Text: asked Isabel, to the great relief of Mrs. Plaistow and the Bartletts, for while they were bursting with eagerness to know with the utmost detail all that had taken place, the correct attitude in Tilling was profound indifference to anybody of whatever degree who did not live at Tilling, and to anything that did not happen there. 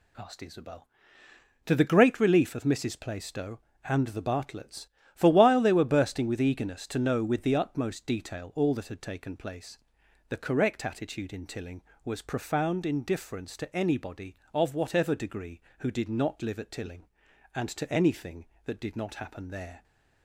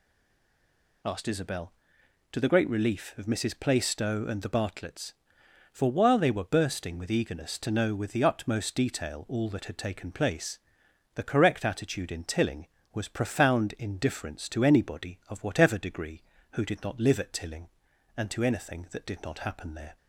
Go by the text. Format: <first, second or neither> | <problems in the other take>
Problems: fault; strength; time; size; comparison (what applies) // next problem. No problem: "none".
first | stays silent before the first word; until 1.0 s; 1.0 s long